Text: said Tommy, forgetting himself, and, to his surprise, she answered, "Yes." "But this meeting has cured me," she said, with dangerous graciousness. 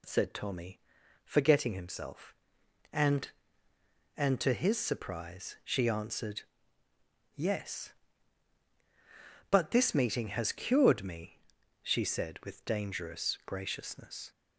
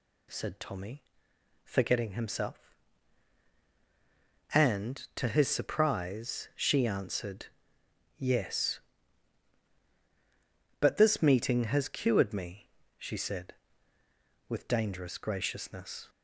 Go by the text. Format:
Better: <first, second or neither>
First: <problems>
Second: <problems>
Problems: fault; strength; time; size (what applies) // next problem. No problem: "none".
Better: second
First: says "and" twice; at 4.1 s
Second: none